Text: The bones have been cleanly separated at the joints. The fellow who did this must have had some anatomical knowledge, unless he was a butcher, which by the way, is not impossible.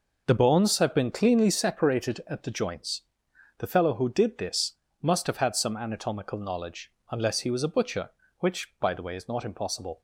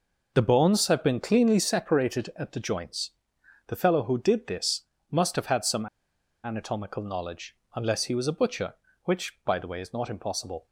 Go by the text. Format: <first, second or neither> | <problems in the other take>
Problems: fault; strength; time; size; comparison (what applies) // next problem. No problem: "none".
first | pauses between "this" and "must"; slight; at 4.8 s; 0.28 s long; slight in the first // pauses between "some" and "anatomical"; noticeable; at 5.8 s; 0.57 s long